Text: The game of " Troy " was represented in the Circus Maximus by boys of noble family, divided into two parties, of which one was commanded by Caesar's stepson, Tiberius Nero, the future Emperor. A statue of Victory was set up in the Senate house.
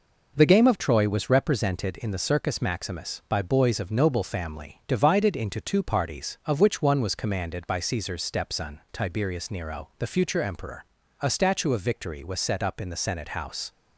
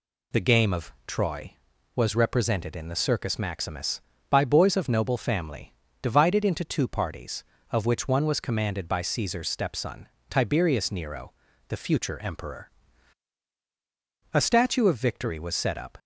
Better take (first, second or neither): first